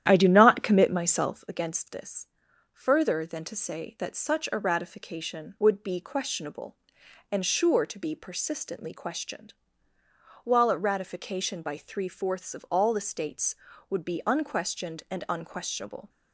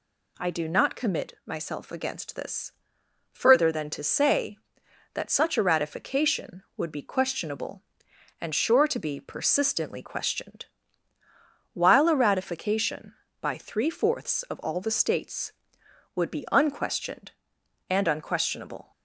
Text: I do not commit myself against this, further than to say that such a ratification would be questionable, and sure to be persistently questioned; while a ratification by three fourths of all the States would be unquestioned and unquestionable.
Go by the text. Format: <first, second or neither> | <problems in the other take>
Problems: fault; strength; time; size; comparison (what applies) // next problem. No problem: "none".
second | starts louder than the rest; strong; until 1.5 s; 11 dB